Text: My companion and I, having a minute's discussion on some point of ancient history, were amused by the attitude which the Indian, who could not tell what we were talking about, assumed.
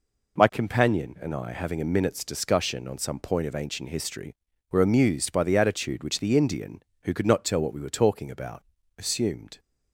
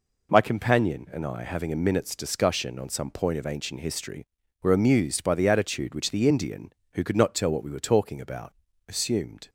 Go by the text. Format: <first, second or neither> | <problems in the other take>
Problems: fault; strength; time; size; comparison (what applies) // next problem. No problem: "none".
neither | none